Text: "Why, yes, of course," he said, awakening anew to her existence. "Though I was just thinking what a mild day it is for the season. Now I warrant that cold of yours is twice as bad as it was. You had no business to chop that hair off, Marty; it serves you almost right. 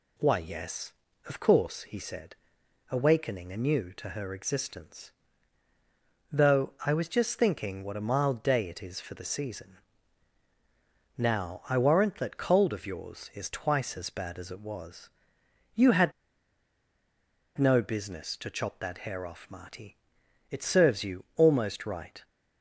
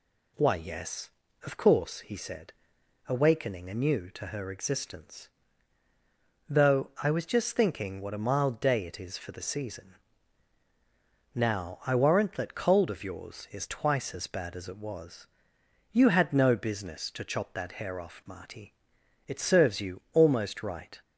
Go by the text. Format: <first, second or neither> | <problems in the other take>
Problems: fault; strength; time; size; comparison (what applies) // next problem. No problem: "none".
second | pauses between "had" and "no"; strong; at 16.1 s; 1.4 s long